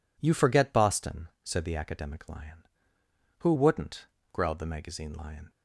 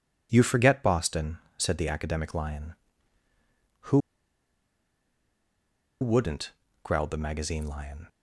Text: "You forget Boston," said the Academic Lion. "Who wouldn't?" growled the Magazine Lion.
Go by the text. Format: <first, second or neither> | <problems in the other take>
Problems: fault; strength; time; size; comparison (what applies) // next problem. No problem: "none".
first | pauses between "Who" and "wouldn't"; strong; at 3.9 s; 2.0 s long